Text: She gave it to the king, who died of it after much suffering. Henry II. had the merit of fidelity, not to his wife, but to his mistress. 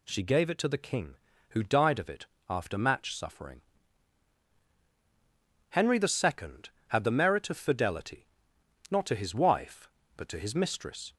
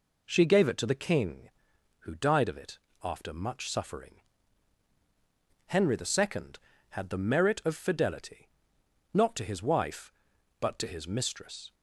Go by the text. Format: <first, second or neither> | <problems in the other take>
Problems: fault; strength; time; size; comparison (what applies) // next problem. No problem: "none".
second | pauses between "it" and "after"; slight; at 2.2 s; 0.24 s long; slight in the second // says "match" for "much"; at 2.7 s